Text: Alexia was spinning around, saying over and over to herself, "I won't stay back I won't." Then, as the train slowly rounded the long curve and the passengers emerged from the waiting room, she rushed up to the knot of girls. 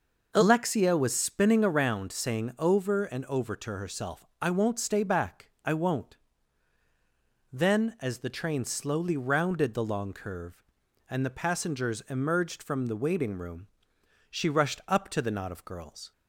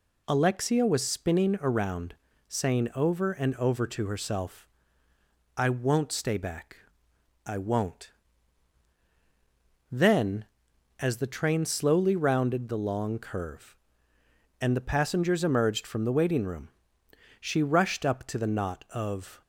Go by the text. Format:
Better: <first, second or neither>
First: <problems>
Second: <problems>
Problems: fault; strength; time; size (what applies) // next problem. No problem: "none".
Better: first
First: pauses between "back" and "I"; slight; at 5.4 s; 0.16 s long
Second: pauses between "back" and "I"; noticeable; at 6.7 s; 0.68 s long // stops before "girls"; at 19.4 s